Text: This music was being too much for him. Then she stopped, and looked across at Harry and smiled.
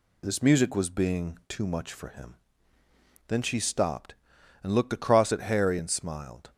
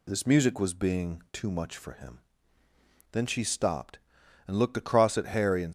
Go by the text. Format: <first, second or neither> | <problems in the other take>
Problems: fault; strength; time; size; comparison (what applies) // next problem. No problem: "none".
first | stops before "smiled"; at 5.6 s